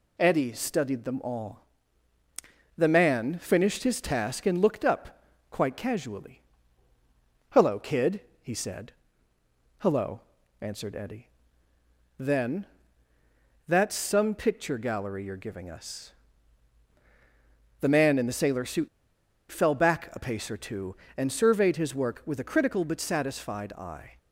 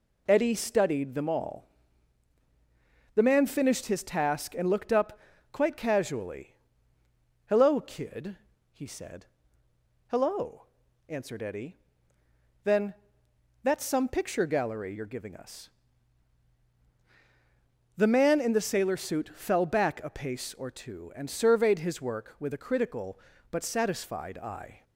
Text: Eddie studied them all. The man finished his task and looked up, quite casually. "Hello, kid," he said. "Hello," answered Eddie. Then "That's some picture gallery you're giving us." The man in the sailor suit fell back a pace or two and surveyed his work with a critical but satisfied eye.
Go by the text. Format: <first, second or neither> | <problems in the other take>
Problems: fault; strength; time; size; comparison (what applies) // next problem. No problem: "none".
second | pauses between "Then" and "That's"; at 12.6 s; 1.0 s long; noticeable in the second // pauses between "suit" and "fell"; noticeable; at 18.8 s; 0.62 s long